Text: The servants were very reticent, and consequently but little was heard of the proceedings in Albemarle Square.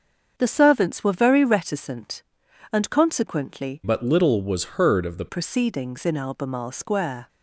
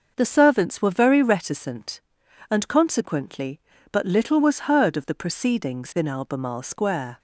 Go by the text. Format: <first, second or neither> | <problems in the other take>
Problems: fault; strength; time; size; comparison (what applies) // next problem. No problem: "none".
second | starts louder than the rest; until 1.3 s; 6.5 dB; noticeable in the second // changes voice from "but" to "the"; from 3.8 to 5.2 s; 1.4 s long